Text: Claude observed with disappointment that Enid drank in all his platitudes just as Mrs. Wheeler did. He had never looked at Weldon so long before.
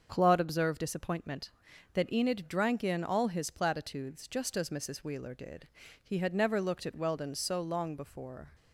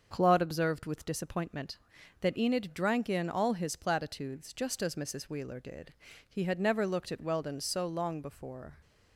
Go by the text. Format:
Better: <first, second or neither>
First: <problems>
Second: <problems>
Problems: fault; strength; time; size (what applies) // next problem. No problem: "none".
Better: second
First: starts louder than the rest; until 1.1 s; 6.5 dB // skips "with"; at 0.8 s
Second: starts louder than the rest; until 1.1 s; 6.5 dB